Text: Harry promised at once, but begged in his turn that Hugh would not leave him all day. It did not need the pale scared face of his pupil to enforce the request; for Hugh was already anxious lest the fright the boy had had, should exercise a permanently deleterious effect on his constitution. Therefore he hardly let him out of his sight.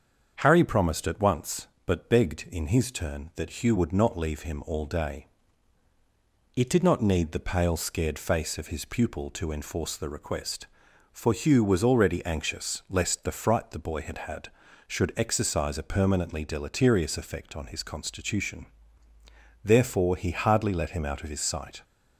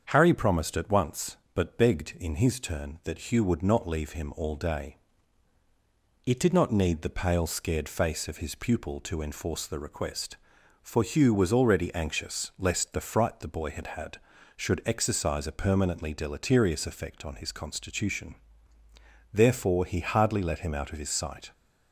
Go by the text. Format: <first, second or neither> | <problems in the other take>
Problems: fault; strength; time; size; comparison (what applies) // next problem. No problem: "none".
neither | starts louder than the rest; strong; the same in both